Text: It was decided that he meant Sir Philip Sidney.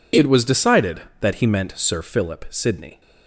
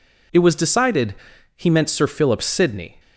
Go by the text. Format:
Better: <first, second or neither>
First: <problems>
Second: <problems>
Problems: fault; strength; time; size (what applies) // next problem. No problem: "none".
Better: first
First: none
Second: skips "that"; at 1.3 s